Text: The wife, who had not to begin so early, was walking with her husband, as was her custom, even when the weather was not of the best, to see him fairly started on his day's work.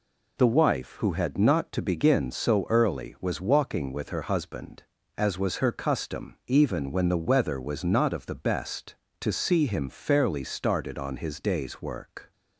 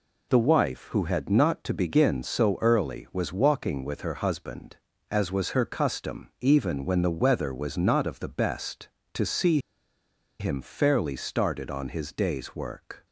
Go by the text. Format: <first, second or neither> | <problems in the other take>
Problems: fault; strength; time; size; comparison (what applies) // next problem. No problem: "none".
first | pauses between "see" and "him"; noticeable; at 9.5 s; 0.81 s long